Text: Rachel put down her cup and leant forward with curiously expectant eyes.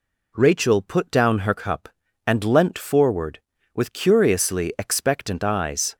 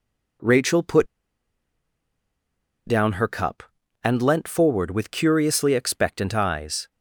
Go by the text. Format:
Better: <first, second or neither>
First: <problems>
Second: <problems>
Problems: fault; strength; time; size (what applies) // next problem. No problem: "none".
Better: first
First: none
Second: pauses between "put" and "down"; strong; at 1.0 s; 1.7 s long